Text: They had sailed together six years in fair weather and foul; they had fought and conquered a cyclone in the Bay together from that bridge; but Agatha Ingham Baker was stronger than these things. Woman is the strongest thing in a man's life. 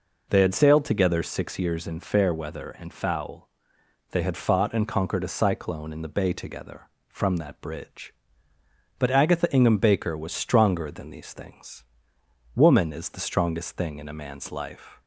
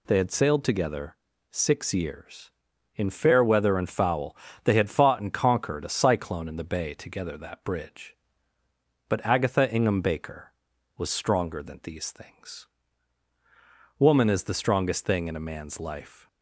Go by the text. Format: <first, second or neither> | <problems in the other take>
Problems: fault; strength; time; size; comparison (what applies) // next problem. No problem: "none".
first | pauses between "together" and "six"; slight; at 1.1 s; 0.36 s long // skips "from"; at 7.3 s